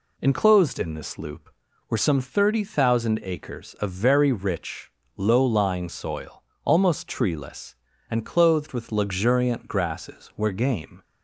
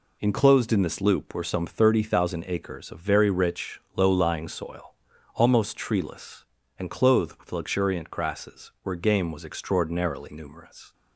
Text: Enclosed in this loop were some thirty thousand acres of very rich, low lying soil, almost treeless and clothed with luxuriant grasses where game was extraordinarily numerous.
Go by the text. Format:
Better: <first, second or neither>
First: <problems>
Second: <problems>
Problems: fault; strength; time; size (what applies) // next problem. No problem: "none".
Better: second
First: stops before "was extraordinarily numerous"; at 11.0 s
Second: none